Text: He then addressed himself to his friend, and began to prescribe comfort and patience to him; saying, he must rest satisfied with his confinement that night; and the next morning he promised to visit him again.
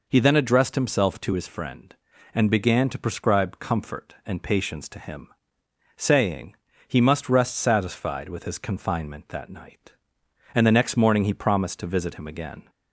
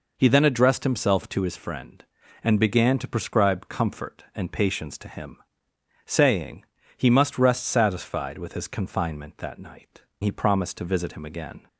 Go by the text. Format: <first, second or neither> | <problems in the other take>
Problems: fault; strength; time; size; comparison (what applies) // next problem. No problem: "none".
first | skips "and the next morning"; at 10.1 s